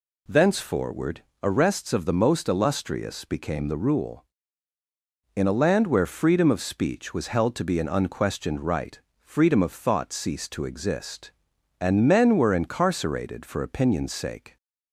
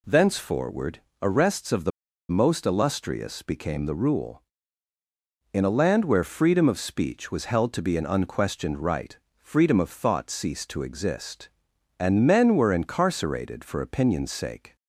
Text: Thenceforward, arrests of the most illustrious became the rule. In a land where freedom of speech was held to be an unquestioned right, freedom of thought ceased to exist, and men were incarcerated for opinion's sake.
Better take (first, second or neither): first